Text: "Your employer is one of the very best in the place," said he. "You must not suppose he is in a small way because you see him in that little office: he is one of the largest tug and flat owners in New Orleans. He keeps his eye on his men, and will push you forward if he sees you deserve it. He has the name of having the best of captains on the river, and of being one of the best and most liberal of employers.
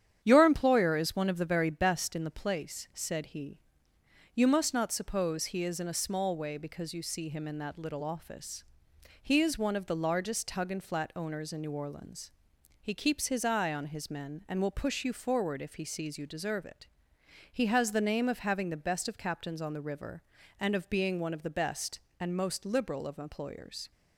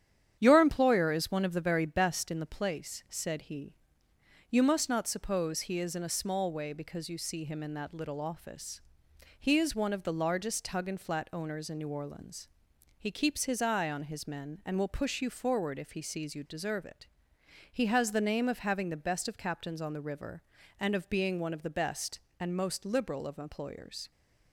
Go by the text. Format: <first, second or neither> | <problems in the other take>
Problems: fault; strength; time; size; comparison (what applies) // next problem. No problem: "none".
neither | starts louder than the rest; strong; the same in both